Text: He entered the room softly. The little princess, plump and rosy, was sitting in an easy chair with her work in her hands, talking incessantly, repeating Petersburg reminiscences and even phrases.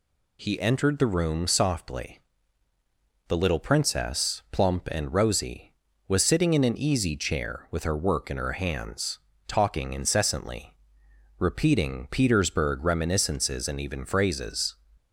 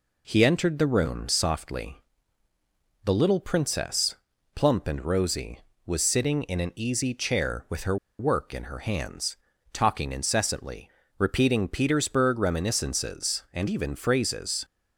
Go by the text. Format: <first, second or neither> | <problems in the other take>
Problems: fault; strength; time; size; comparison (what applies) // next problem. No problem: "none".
first | pauses between "her" and "work"; slight; at 7.9 s; 0.23 s long